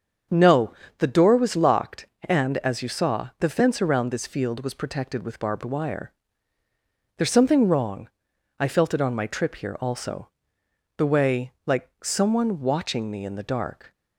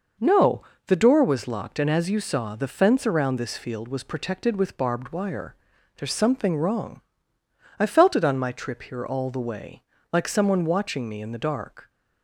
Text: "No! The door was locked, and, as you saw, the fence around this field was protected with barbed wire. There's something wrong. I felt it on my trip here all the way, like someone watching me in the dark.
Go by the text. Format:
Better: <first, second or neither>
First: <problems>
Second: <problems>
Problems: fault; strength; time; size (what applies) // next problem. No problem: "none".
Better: second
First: starts louder than the rest; strong; until 1.5 s; 7 dB // says "also" for "all"; at 9.7 s // pauses between "like" and "someone"; slight; at 11.8 s; 0.16 s long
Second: none